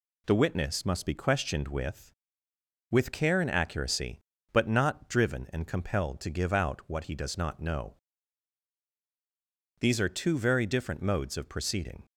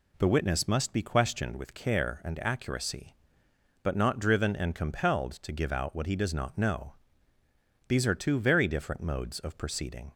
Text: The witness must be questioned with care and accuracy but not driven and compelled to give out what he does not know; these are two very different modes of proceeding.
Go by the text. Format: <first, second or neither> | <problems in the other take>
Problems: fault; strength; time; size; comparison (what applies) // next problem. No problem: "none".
second | says "with" twice; at 2.8 s